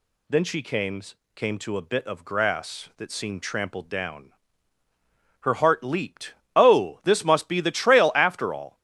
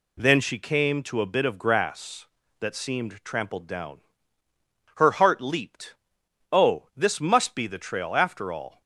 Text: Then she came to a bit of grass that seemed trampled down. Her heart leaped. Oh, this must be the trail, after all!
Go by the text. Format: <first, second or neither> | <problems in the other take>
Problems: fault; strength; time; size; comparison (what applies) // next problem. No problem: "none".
second | says "came" twice; at 1.3 s